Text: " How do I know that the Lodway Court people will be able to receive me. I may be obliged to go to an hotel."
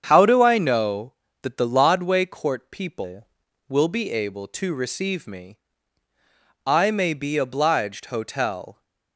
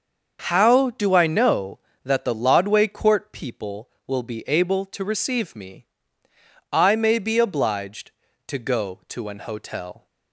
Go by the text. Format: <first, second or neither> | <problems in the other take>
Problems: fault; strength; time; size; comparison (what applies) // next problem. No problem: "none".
second | starts louder than the rest; strong; until 1.0 s; 7.5 dB; also in the second // skips "to go to an"; at 8.0 s